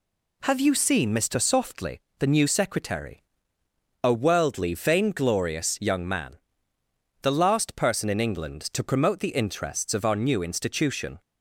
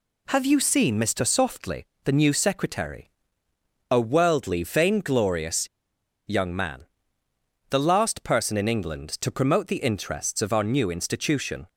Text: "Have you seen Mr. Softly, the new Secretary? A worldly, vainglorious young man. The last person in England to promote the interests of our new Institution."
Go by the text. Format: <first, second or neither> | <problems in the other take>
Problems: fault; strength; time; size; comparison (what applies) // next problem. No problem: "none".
first | pauses between "vainglorious" and "young"; noticeable; at 5.6 s; 0.60 s long